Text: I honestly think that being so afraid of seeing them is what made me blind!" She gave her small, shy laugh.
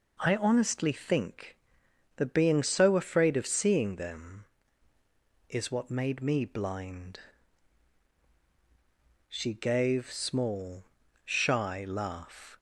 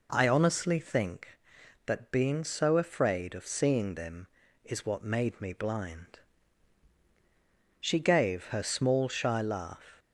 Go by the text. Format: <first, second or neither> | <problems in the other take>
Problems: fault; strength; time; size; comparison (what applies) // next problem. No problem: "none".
second | skips "her"; at 10.1 s